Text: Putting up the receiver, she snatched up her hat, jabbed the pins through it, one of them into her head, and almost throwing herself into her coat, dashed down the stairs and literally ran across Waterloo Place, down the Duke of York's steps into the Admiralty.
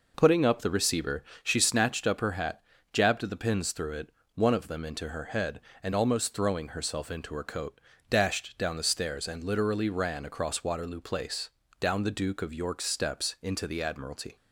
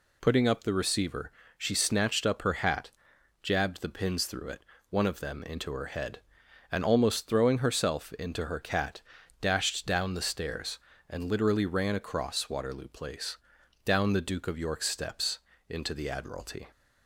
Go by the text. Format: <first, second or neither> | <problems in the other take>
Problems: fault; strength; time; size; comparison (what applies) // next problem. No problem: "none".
first | says "cat" for "coat"; at 8.5 s // pauses between "steps" and "into"; slight; at 15.3 s; 0.30 s long